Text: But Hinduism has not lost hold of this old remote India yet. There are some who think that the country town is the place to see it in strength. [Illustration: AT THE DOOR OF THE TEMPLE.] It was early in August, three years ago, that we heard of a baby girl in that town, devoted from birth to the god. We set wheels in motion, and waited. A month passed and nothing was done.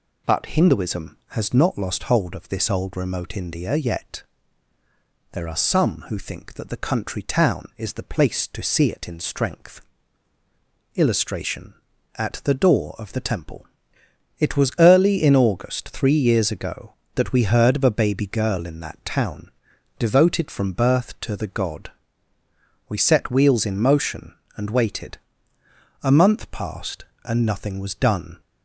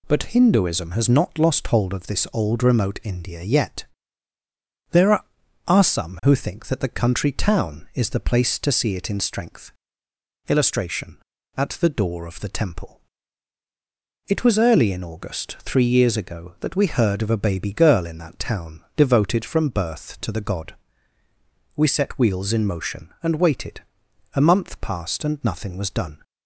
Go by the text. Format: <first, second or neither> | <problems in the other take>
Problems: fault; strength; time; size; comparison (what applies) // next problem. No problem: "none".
first | says "are" twice; at 5.6 s